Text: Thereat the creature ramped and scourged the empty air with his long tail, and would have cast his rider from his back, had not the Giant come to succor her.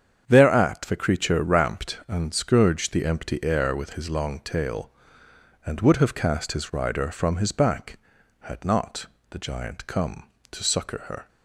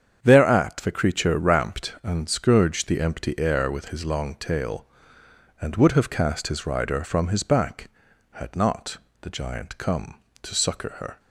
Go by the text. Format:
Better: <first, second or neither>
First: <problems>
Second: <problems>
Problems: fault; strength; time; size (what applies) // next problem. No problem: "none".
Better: neither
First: starts louder than the rest; strong; until 1.2 s; 8 dB // pauses between "not" and "the"; slight; at 9.0 s; 0.24 s long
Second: starts louder than the rest; strong; until 1.2 s; 8 dB // pauses between "not" and "the"; slight; at 8.9 s; 0.24 s long